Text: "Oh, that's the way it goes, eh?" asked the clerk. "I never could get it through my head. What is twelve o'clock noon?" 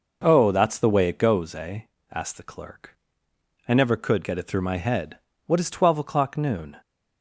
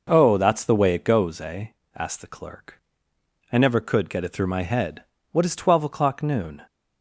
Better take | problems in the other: neither | none

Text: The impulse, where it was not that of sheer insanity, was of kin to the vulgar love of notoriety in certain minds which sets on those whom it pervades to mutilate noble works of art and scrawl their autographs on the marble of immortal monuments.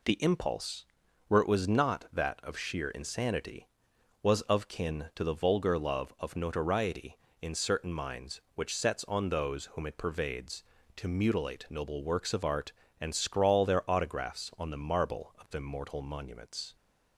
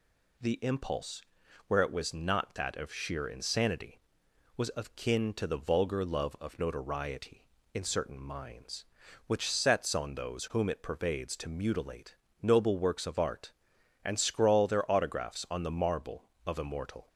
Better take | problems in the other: first | pauses between "mutilate" and "noble"; slight; at 12.1 s; 0.28 s long // stops before "monuments"; at 17.0 s

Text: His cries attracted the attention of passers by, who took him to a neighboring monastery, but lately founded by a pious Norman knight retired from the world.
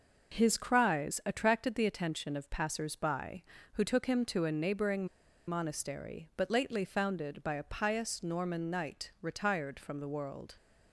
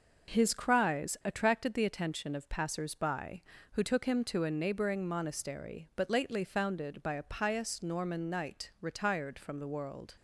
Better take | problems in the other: second | pauses between "neighboring" and "monastery"; at 5.0 s; 0.41 s long

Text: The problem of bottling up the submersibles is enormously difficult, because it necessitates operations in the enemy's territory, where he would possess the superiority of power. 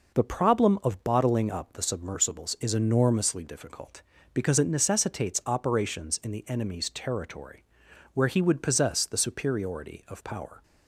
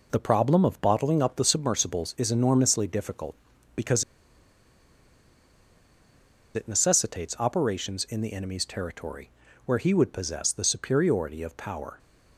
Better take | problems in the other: first | pauses between "because" and "it"; strong; at 4.0 s; 2.5 s long

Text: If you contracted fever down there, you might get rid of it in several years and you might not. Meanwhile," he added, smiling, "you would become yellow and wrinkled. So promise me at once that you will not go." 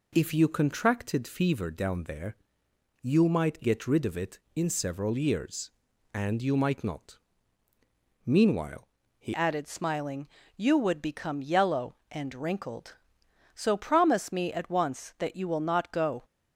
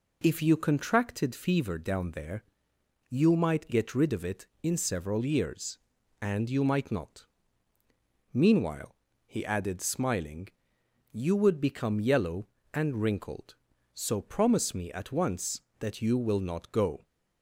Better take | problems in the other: second | changes voice at "added"; from 9.3 s on; 6.9 s long

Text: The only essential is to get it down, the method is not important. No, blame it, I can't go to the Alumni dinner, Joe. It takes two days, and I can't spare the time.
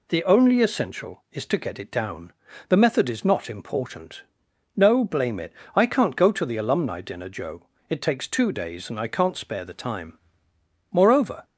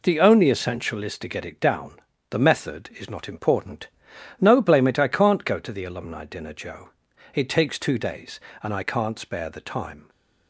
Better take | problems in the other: second | goes on to say "Moreover"; from 10.9 s on; 0.52 s long

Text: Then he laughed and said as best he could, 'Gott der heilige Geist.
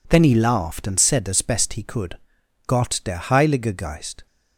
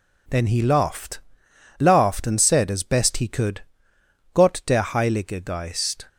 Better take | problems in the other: first | says "laughed" twice; at 1.7 s

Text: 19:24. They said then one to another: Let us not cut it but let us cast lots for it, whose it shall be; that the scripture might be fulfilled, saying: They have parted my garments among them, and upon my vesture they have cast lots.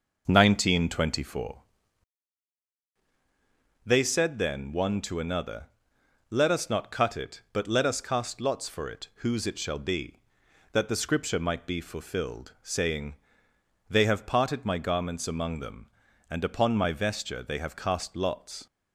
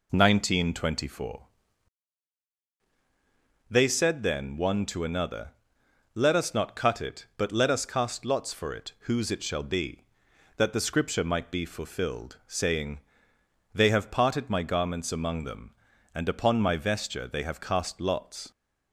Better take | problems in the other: second | starts louder than the rest; noticeable; until 1.8 s; 6 dB

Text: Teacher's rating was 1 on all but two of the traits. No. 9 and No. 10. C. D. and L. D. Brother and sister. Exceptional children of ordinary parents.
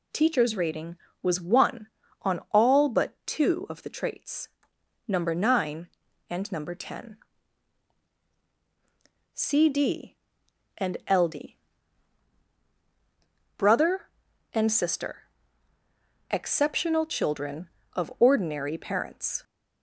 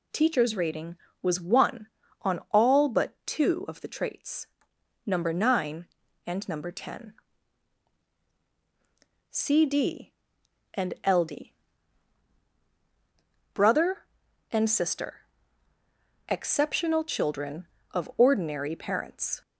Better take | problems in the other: neither | pauses between "D" and "Brother"; strong; the same in both

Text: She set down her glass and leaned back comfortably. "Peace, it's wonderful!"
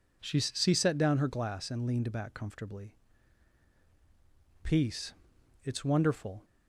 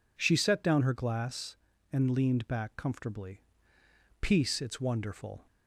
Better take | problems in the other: second | says "She" twice; at 0.3 s

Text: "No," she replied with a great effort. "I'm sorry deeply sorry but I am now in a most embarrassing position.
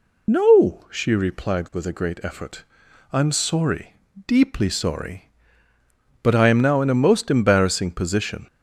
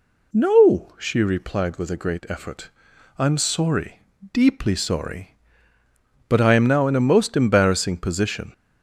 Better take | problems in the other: second | loses the start of "No"; at 0.2 s; 30 ms // pauses between "sorry" and "deeply"; slight; at 3.9 s; 0.32 s long; slight in the second

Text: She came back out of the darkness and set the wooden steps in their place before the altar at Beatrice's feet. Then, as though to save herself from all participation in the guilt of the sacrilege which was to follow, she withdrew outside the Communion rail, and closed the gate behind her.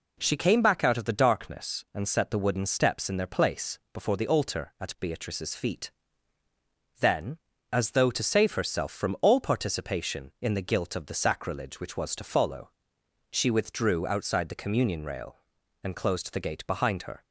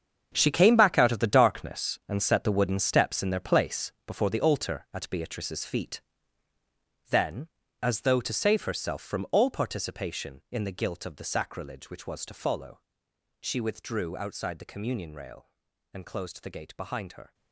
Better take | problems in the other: first | gets quieter; strong; throughout; 12.5 dB

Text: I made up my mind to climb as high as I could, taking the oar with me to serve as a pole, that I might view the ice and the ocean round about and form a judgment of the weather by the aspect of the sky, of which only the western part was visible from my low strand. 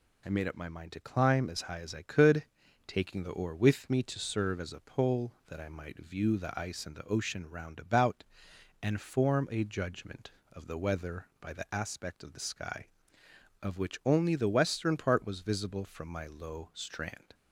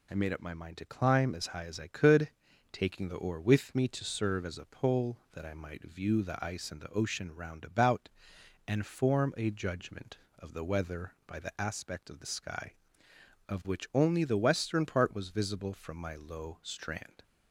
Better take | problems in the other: neither | none

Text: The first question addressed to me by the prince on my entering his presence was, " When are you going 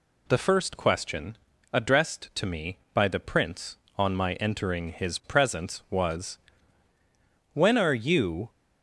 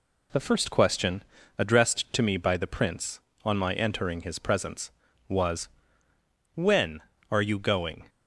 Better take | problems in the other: second | pauses between "question" and "addressed"; slight; at 1.3 s; 0.36 s long; slight in the second // stops before "going"; at 8.4 s

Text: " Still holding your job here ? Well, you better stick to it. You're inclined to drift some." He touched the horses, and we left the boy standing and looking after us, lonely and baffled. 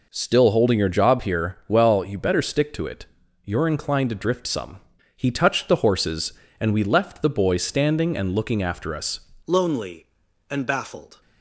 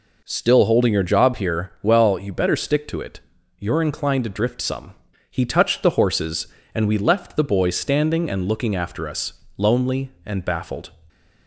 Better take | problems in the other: second | changes voice at "lonely"; from 9.4 s on; 1.8 s long

